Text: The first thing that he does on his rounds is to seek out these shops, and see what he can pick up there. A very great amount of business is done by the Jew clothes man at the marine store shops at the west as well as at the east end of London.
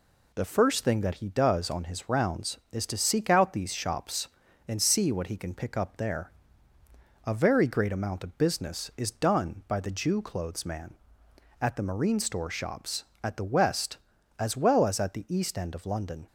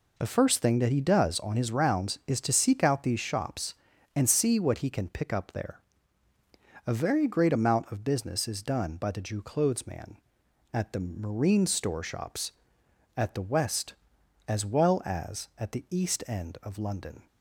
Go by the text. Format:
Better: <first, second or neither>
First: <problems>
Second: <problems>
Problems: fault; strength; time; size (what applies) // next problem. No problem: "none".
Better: neither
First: none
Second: none